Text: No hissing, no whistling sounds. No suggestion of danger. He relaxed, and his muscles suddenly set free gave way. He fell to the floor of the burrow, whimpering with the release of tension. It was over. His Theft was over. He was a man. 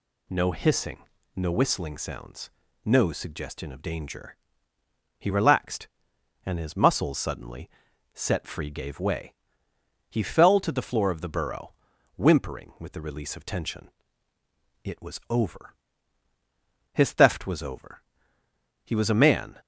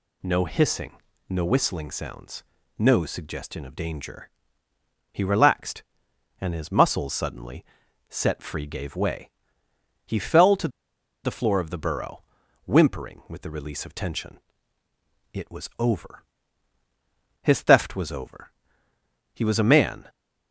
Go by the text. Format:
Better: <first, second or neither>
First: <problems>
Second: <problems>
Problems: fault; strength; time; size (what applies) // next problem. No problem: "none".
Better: first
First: pauses between "suddenly" and "set"; noticeable; at 7.6 s; 0.46 s long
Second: pauses between "suddenly" and "set"; noticeable; at 7.6 s; 0.46 s long // pauses between "to" and "the"; noticeable; at 10.6 s; 0.55 s long